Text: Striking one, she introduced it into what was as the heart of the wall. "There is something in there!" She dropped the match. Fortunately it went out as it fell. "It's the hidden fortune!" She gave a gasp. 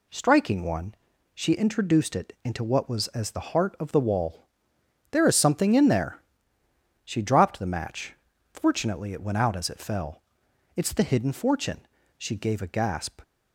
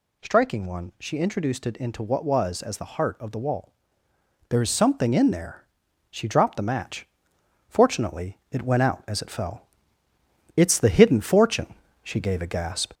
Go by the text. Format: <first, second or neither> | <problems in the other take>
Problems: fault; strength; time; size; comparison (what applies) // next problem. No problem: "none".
first | gets louder; slight; throughout; 2 dB